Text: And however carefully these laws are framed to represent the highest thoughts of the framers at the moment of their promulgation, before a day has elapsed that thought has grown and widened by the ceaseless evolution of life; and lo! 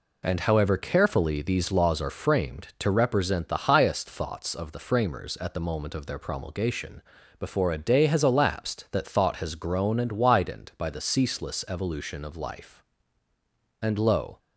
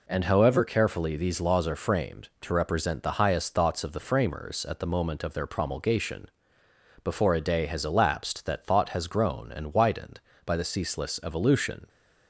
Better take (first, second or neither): first